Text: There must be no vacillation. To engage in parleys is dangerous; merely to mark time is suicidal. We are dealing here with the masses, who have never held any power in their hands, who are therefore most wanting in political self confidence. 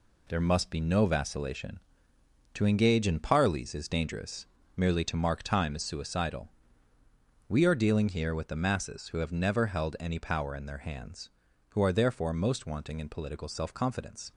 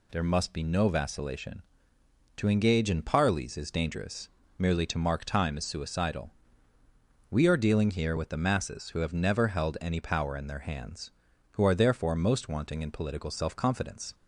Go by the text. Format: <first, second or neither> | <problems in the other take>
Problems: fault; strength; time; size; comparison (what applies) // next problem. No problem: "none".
second | gets quieter; throughout; 7 dB